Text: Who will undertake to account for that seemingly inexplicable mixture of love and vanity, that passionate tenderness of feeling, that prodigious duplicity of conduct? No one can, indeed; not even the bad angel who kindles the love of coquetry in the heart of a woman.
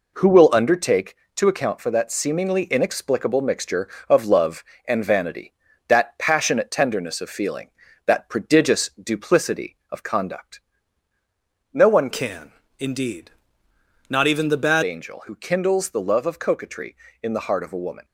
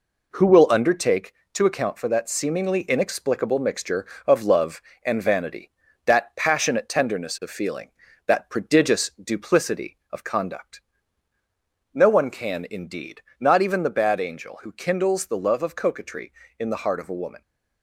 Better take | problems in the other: second | changes voice from "can" to "bad"; from 12.1 to 14.8 s; 2.7 s long

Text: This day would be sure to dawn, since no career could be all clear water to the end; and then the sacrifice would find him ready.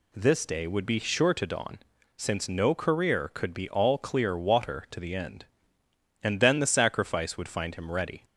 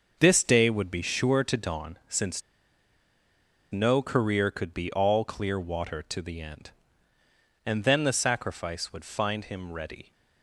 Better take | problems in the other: first | starts louder than the rest; until 1.2 s; 6.5 dB // pauses between "since" and "no"; strong; at 2.4 s; 1.3 s long

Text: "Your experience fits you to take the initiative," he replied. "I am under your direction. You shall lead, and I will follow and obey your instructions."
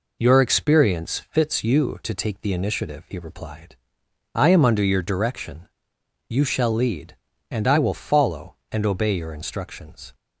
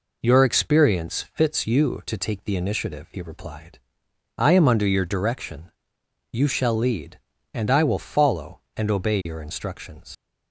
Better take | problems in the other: first | leaves "instructions" unfinished; at 10.1 s; 80 ms

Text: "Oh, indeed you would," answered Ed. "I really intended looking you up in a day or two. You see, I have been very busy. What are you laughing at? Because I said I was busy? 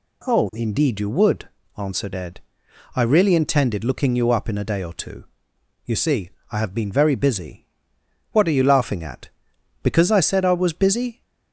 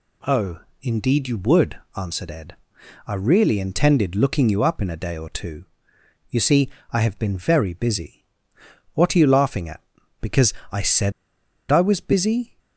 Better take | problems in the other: first | pauses between "Because" and "I"; slight; at 10.5 s; 0.18 s long // pauses between "said" and "I"; noticeable; at 11.1 s; 0.59 s long

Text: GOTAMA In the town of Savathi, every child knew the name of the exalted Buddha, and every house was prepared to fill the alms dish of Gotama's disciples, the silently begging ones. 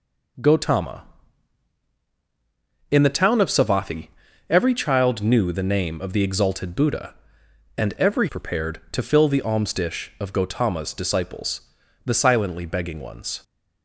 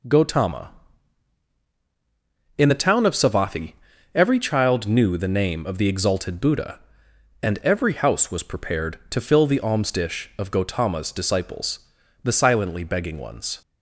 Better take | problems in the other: second | skips "house was"; at 8.2 s

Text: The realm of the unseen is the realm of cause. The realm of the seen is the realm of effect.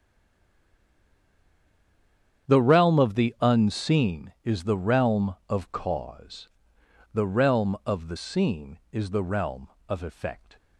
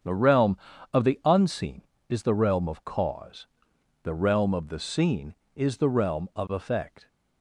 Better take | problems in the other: second | stays silent before the first word; until 2.4 s; 2.4 s long // starts louder than the rest; strong; until 3.5 s; 8.5 dB; strong in the second

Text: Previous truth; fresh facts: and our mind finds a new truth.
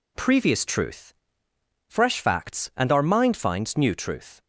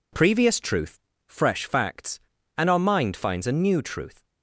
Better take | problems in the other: second | skips "a"; at 3.7 s

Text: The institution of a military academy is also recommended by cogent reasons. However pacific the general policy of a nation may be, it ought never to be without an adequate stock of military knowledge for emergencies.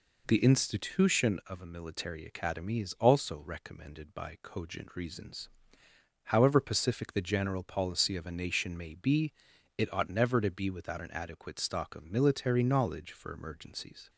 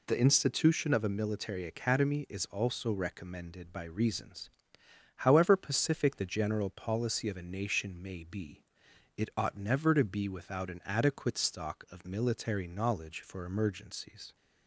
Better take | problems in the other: first | skips "cogent"; at 3.8 s

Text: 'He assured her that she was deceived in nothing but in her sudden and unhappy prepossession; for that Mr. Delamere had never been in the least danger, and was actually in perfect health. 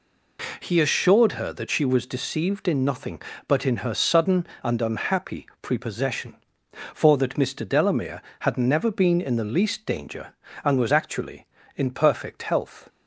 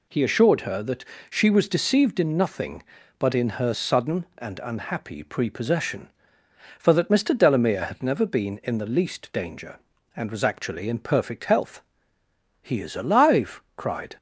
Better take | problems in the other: first | pauses between "that" and "she"; slight; at 1.0 s; 0.26 s long // goes on to say "He is alive cried"; from 12.6 s on; 1.5 s long

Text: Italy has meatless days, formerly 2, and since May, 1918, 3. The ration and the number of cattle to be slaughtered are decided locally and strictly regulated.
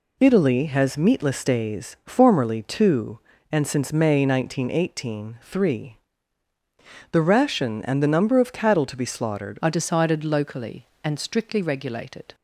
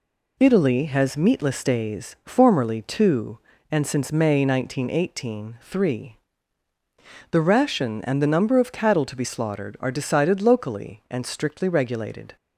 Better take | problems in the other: second | changes voice at "are"; from 9.6 s on; 2.7 s long

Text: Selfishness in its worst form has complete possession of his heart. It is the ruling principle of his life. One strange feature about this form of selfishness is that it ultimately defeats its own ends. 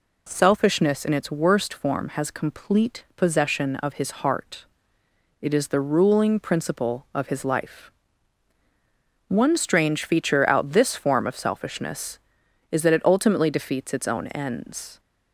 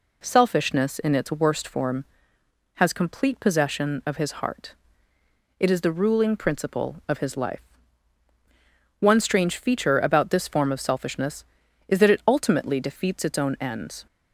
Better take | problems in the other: second | says "out" for "about"; at 10.4 s

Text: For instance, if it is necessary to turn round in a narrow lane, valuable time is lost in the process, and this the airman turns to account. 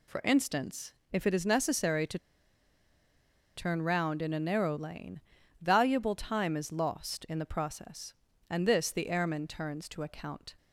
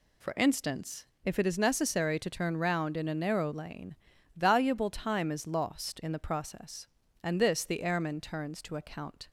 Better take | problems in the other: second | pauses between "to" and "turn"; strong; at 2.1 s; 1.3 s long

